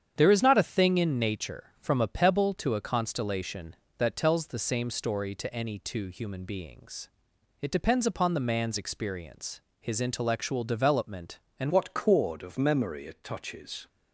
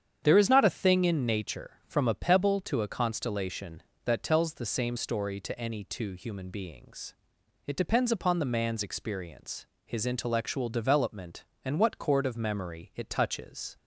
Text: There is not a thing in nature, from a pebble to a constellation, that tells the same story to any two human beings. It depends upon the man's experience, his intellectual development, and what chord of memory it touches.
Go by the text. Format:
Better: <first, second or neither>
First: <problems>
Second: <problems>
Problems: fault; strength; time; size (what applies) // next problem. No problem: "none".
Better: second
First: starts louder than the rest; strong; until 1.1 s; 8.5 dB // changes voice at "what"; from 11.6 s on; 2.2 s long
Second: starts louder than the rest; strong; until 1.2 s; 8.5 dB